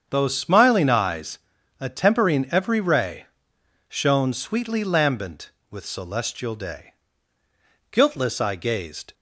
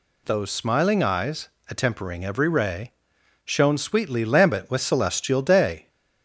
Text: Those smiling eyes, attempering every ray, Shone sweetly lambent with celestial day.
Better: second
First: starts louder than the rest; strong; until 1.1 s; 7.5 dB // goes on to say "Guiltless I gazed"; noticeable; from 7.9 s on; 1.2 s long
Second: none

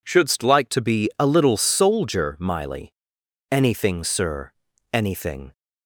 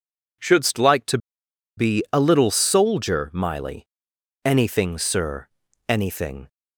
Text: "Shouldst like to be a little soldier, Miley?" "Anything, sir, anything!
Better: first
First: none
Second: pauses between "to" and "be"; noticeable; at 1.1 s; 0.59 s long

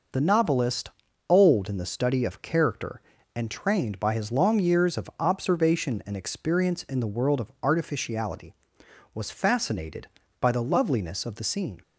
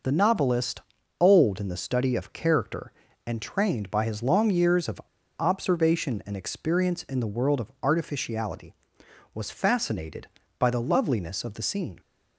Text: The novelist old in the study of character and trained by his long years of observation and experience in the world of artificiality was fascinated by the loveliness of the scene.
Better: first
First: pauses between "novelist" and "old"; at 0.8 s; 0.38 s long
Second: pauses between "novelist" and "old"; at 0.8 s; 0.38 s long // pauses between "of" and "observation"; at 4.9 s; 0.40 s long

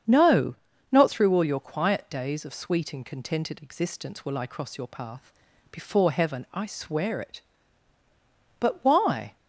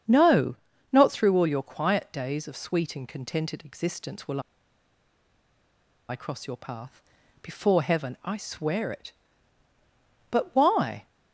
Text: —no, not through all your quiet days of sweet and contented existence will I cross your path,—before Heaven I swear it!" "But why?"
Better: first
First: starts louder than the rest; strong; until 1.4 s; 7.5 dB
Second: starts louder than the rest; strong; until 1.4 s; 7.5 dB // pauses between "will" and "I"; strong; at 4.3 s; 1.6 s long

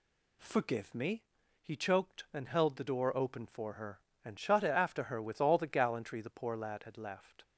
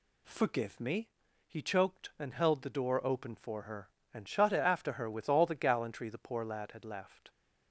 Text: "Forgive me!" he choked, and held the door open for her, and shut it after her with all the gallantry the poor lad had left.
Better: neither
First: none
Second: none

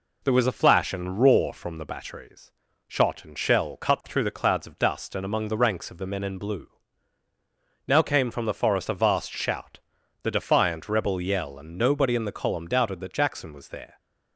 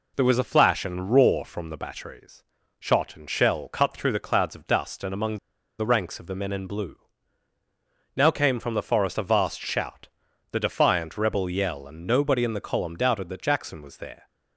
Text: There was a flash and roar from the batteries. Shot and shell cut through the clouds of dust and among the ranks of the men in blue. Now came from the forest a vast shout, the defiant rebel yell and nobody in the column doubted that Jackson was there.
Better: first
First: none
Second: pauses between "among" and "the"; at 5.3 s; 0.41 s long

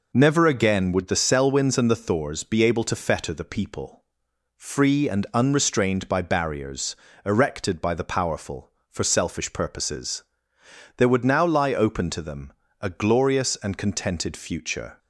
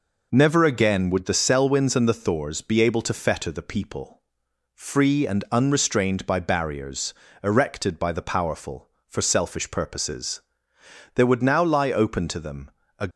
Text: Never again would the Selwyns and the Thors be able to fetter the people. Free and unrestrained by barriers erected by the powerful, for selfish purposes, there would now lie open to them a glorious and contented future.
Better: first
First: pauses between "barriers" and "erected"; slight; at 6.9 s; 0.30 s long // pauses between "them" and "a"; slight; at 12.5 s; 0.28 s long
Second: pauses between "barriers" and "erected"; slight; at 7.1 s; 0.30 s long // pauses between "them" and "a"; slight; at 12.6 s; 0.28 s long // stops before "glorious and contented future"; at 13.1 s

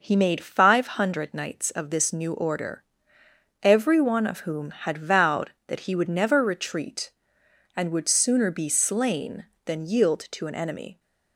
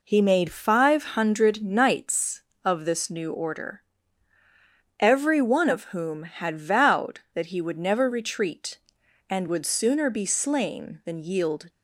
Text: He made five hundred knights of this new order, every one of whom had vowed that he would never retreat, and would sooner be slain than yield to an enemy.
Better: first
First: none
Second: stops before "to an enemy"; at 11.6 s

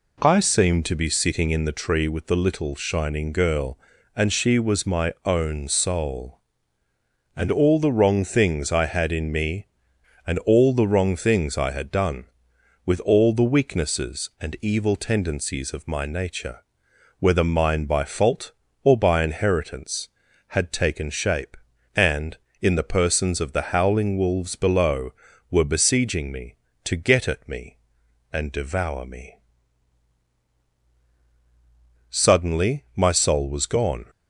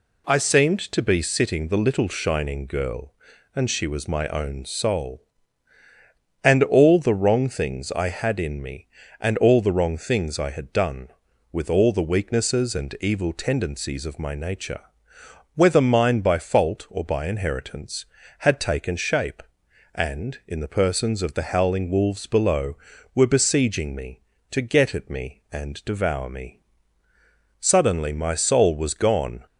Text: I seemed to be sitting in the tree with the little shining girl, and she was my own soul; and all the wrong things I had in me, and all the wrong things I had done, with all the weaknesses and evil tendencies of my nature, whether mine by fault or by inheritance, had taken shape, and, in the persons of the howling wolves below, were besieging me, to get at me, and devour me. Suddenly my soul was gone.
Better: first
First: none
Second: skips "in the tree with"; at 1.6 s

